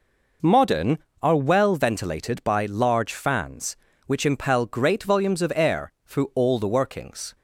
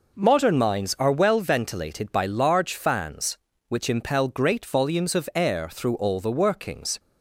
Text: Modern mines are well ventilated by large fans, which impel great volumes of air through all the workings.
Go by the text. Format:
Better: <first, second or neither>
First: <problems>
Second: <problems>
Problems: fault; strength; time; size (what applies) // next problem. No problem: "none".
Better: second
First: skips "mines"; at 1.0 s // pauses between "air" and "through"; slight; at 5.9 s; 0.16 s long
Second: none